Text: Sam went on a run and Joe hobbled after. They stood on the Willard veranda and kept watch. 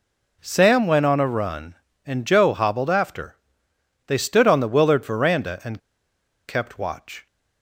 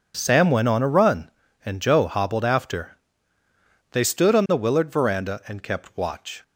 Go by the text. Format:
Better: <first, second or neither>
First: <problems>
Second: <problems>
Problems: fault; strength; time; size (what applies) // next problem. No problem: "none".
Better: second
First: pauses between "and" and "kept"; noticeable; at 5.8 s; 0.68 s long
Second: none